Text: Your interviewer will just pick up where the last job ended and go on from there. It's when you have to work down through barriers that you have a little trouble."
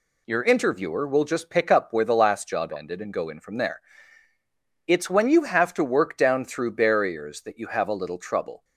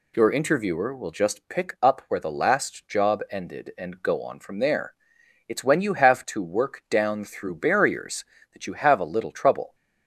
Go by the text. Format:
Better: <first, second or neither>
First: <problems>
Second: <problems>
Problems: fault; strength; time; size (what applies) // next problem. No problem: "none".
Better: second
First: says "in" for "on"; at 3.2 s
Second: none